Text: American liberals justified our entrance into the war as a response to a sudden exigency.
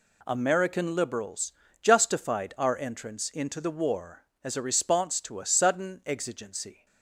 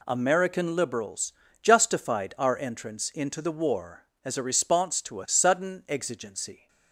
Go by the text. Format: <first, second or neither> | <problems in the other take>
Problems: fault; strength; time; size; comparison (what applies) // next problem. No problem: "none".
neither | pauses between "liberals" and "justified"; slight; the same in both